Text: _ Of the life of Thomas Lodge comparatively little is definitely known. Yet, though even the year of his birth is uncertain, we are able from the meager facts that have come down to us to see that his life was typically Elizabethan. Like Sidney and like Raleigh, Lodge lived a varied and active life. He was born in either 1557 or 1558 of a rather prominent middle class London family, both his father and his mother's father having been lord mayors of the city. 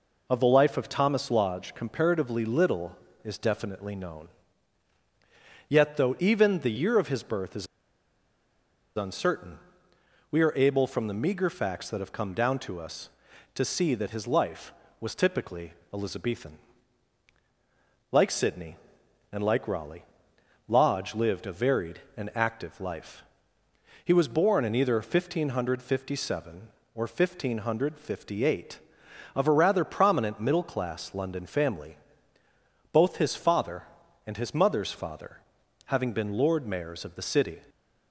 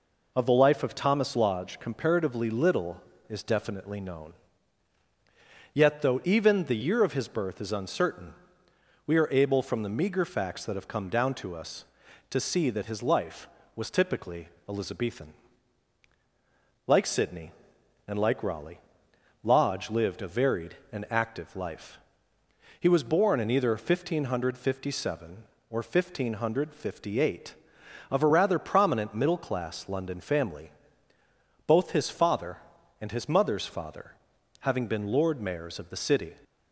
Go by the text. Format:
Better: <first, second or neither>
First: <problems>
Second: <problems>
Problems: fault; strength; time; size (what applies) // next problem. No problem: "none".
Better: second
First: pauses between "is" and "uncertain"; strong; at 7.6 s; 1.3 s long // pauses between "typically" and "Elizabethan"; slight; at 15.7 s; 0.20 s long // pauses between "father" and "having"; noticeable; at 35.3 s; 0.48 s long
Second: pauses between "typically" and "Elizabethan"; slight; at 14.4 s; 0.20 s long // pauses between "father" and "having"; noticeable; at 34.1 s; 0.48 s long